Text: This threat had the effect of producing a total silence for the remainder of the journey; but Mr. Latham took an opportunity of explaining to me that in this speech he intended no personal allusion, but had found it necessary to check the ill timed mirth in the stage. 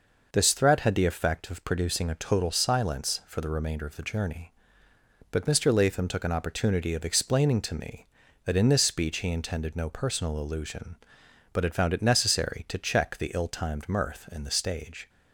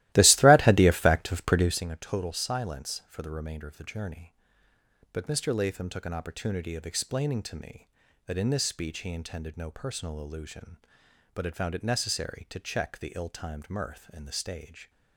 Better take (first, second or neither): first